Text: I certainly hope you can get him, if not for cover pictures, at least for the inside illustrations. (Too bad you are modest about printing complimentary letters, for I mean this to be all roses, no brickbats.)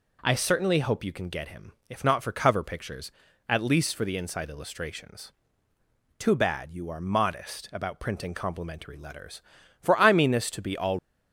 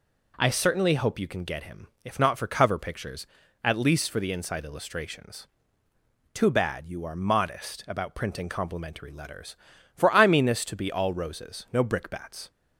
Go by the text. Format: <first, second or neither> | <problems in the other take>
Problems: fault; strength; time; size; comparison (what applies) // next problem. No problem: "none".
second | stops before "roses no brickbats"; at 10.9 s